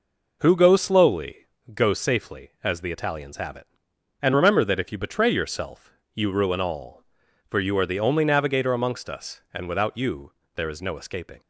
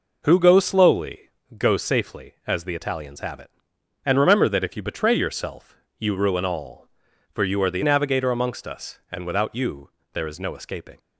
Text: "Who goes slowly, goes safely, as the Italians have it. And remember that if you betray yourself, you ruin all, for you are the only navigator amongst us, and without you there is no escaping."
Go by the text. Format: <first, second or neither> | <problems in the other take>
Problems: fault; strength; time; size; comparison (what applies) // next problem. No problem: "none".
first | skips "only"; at 7.8 s // pauses between "you" and "there"; slight; at 9.8 s; 0.24 s long; slight in the first